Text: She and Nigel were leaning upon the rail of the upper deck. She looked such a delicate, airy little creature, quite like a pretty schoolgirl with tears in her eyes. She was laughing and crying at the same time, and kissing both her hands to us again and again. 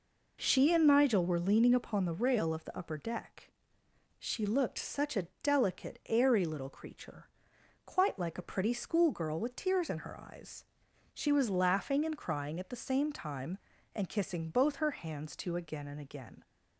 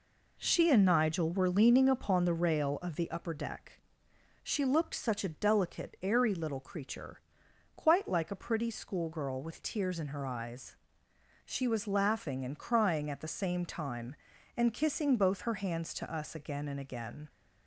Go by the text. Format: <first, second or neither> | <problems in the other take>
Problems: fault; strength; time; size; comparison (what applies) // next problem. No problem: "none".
second | pauses between "a" and "delicate"; slight; at 5.2 s; 0.16 s long // skips "us"; at 15.5 s